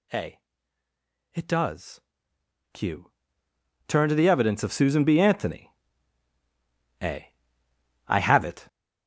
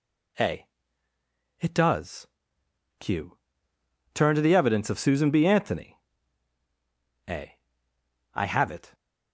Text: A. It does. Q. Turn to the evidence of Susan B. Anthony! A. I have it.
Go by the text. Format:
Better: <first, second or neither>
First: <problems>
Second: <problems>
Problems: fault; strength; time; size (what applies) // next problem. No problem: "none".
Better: second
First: gets louder; strong; throughout; 10.5 dB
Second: none